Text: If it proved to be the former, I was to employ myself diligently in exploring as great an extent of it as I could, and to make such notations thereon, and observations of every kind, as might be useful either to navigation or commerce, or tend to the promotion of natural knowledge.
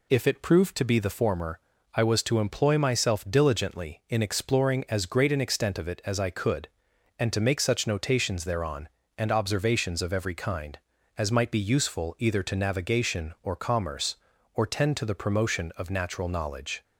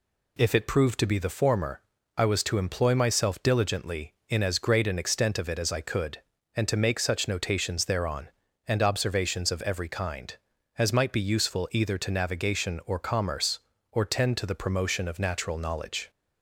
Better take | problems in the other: first | skips "exploring"; at 4.4 s

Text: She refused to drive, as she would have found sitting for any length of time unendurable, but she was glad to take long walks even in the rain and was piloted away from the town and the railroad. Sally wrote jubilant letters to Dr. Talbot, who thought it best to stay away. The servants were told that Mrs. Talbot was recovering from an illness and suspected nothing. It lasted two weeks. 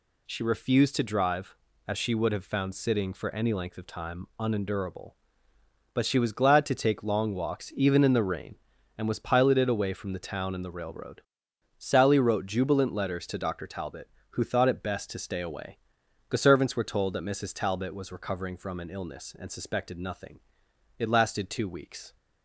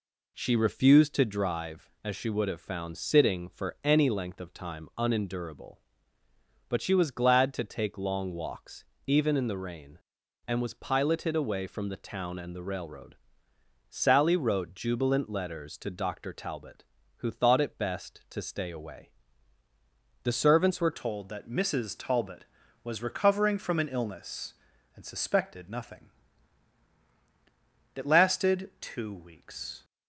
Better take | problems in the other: first | pauses between "walks" and "even"; slight; at 8.8 s; 0.22 s long // changes voice at "told"; from 20.9 s on; 8.9 s long

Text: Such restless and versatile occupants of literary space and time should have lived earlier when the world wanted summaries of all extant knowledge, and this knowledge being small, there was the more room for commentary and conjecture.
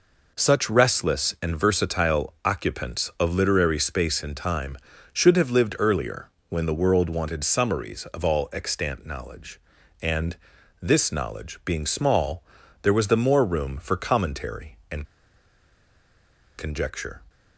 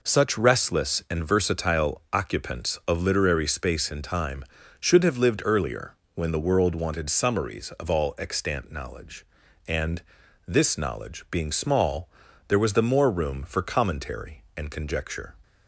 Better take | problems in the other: second | pauses between "earlier" and "when"; slight; at 6.2 s; 0.20 s long; slight in the second // pauses between "and" and "this"; noticeable; at 10.3 s; 0.46 s long; noticeable in the second // pauses between "and" and "conjecture"; strong; at 15.0 s; 1.5 s long

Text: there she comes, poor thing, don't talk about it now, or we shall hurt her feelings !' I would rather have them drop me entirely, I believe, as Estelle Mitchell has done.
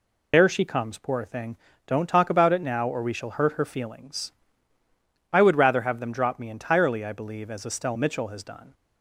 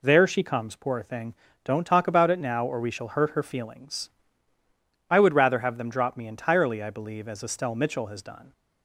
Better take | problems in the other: second | loses the start of "there"; at 0.3 s; 90 ms

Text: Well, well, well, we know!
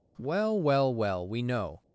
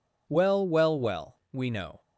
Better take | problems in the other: neither | none

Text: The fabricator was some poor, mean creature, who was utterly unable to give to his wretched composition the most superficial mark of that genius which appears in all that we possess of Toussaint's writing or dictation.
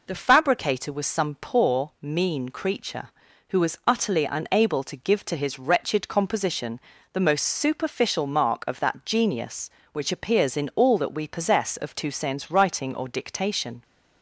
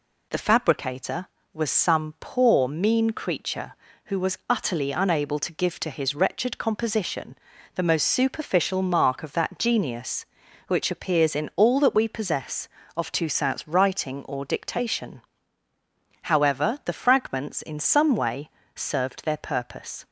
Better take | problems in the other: first | pauses between "composition" and "the"; at 7.3 s; 0.38 s long; slight in the first // goes on to say "However the fragments in some way served their purpose"; strong; from 16.2 s on; 3.8 s long

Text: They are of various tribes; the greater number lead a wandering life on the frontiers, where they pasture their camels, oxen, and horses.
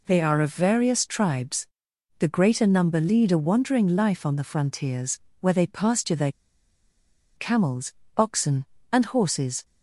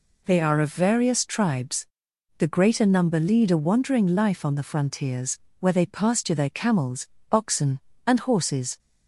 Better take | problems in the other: second | pauses between "their" and "camels"; at 6.3 s; 1.0 s long

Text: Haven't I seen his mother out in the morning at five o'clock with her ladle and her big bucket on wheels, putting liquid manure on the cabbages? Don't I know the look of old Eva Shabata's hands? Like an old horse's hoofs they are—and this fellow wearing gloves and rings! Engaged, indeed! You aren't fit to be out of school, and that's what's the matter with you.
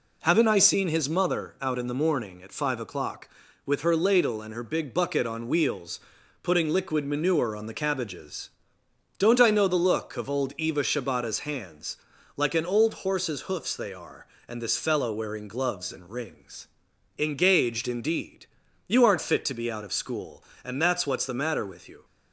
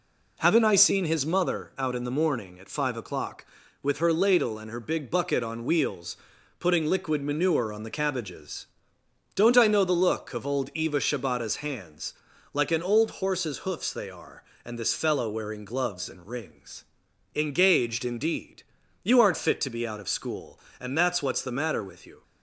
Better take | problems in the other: neither | none

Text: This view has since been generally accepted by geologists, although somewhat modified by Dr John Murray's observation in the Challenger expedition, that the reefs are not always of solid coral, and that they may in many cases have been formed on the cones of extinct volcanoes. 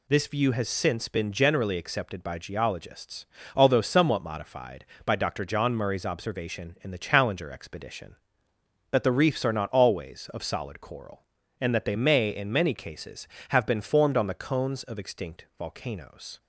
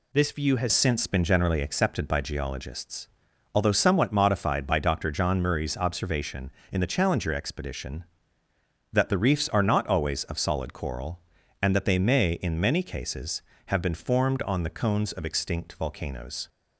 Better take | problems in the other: first | changes voice at "since"; from 0.7 s on; 15.7 s long

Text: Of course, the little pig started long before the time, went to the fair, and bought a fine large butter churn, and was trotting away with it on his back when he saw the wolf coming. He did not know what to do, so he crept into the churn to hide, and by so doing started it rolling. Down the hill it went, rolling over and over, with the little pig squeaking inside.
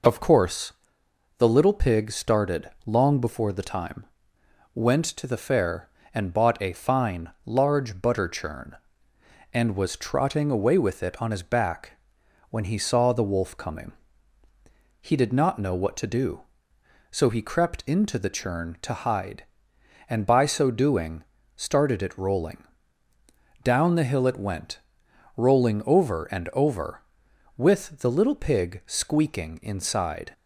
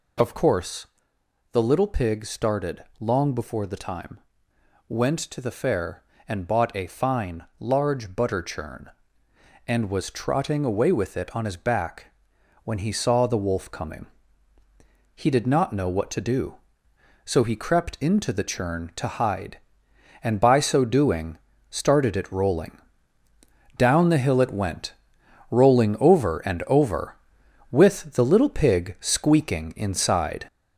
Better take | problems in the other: first | gets louder; noticeable; throughout; 4.5 dB // pauses between "started" and "long"; slight; at 2.8 s; 0.16 s long; slight in the first // pauses between "fine" and "large"; slight; at 7.4 s; 0.16 s long; slight in the first // pauses between "back" and "when"; noticeable; at 12.0 s; 0.58 s long; noticeable in the first // pauses between "doing" and "started"; slight; at 21.3 s; 0.34 s long; slight in the first

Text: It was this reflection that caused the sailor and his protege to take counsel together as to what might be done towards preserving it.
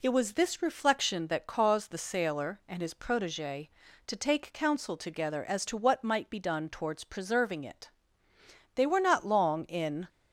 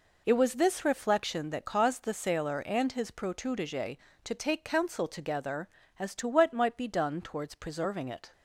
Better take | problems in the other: second | goes on to say "They were not long in"; from 8.7 s on; 1.3 s long

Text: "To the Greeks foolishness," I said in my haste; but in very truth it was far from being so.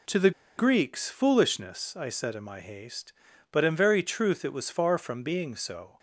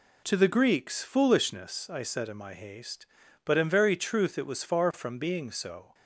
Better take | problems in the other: second | pauses between "the" and "Greeks"; slight; at 0.3 s; 0.27 s long

